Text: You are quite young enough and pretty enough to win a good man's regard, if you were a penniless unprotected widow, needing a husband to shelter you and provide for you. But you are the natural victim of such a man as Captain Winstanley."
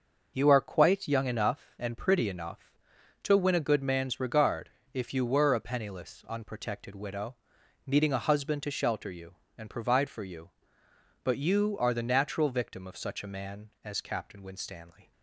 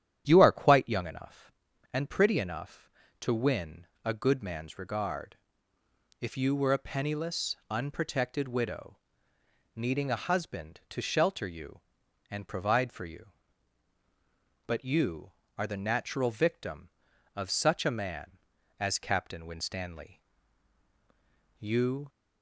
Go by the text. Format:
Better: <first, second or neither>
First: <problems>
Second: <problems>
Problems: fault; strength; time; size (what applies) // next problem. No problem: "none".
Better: first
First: none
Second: starts louder than the rest; strong; until 1.2 s; 10 dB // pauses between "win" and "a"; slight; at 3.8 s; 0.18 s long // goes on to say "You"; from 21.5 s on; 0.50 s long